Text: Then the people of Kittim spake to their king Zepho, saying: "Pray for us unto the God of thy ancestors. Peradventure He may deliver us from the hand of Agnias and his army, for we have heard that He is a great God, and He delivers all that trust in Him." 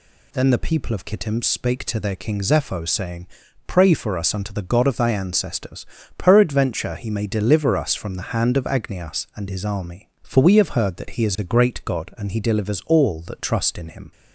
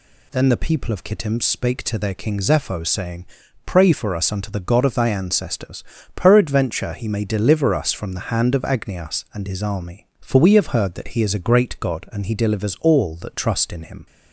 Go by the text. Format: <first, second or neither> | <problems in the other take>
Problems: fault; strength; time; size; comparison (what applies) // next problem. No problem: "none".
neither | none